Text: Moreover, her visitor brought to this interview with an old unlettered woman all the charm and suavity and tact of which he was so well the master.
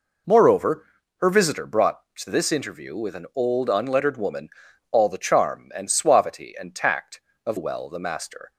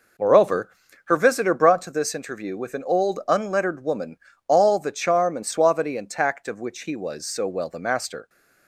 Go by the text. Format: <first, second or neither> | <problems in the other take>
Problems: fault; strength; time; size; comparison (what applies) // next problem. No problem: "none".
second | pauses between "woman" and "all"; at 4.4 s; 0.42 s long; slight in the second // skips "which he was so"; at 7.5 s